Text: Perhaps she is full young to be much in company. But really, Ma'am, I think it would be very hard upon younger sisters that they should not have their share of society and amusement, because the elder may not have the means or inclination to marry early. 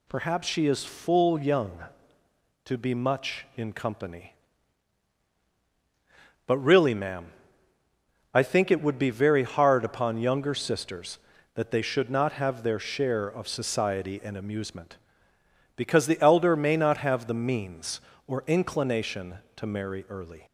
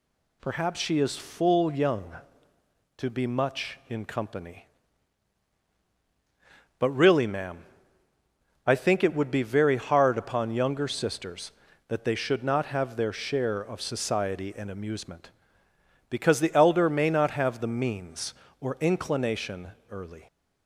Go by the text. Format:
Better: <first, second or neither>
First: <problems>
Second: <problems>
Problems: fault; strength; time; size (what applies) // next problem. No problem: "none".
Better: first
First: none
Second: skips "to marry"; at 19.7 s